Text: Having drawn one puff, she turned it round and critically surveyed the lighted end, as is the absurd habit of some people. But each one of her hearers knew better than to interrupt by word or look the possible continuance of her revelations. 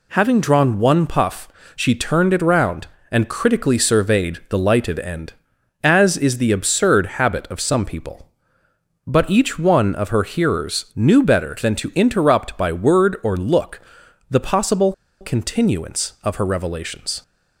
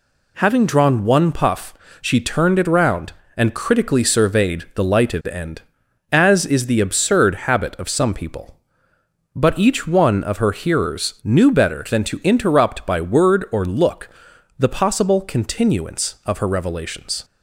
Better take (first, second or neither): second